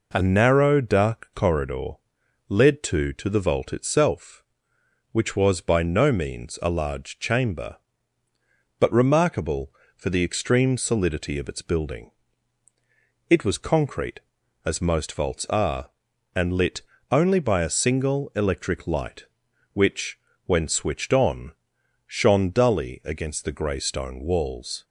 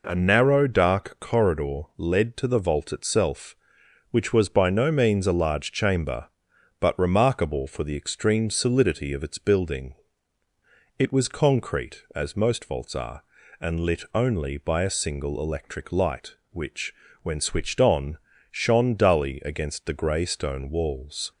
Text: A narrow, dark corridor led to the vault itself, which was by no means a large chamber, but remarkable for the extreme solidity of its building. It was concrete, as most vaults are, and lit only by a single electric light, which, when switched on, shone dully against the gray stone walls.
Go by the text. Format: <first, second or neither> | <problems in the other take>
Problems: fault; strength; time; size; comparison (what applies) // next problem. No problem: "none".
second | pauses between "corridor" and "led"; noticeable; at 1.9 s; 0.54 s long // says "to" twice; at 3.1 s // pauses between "lit" and "only"; slight; at 16.8 s; 0.28 s long